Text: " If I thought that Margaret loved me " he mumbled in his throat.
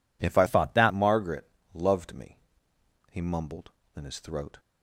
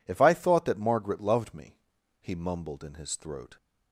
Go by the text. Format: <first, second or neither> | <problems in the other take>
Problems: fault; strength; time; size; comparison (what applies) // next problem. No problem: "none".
second | changes voice from "thought" to "that"; from 0.4 to 0.9 s; 0.5 s long // pauses between "Margaret" and "loved"; slight; at 1.4 s; 0.24 s long